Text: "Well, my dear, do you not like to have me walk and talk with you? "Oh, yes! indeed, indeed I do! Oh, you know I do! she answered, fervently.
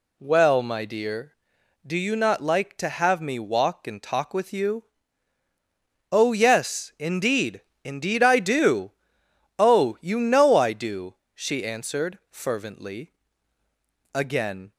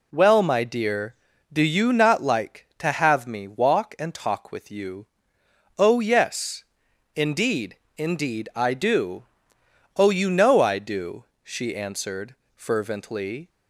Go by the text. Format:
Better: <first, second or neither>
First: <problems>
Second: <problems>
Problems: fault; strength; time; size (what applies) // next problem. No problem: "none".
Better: second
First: goes on to say "Again"; from 14.1 s on; 0.58 s long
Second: none